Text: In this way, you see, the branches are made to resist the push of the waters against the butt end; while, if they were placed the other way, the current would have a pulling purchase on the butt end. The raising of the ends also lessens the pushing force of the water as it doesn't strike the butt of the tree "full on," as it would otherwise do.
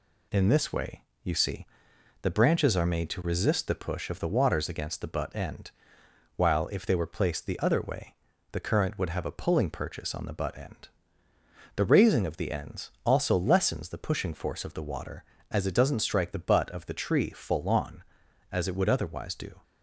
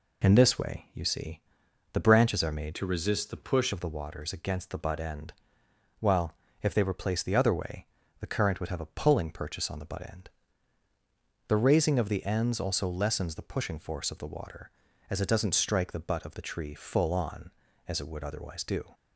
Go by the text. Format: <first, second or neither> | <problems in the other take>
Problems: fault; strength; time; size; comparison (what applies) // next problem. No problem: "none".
first | changes voice from "to" to "push"; from 2.7 to 3.7 s; 1.0 s long